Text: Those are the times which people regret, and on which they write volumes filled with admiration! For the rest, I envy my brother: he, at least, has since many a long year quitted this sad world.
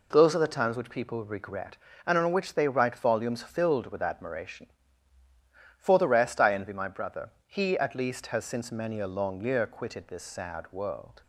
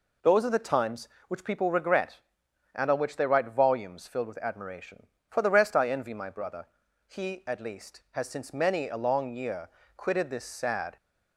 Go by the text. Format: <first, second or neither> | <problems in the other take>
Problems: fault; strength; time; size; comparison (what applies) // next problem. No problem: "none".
first | pauses between "year" and "quitted"; slight; at 9.6 s; 0.28 s long // stops before "world"; at 10.9 s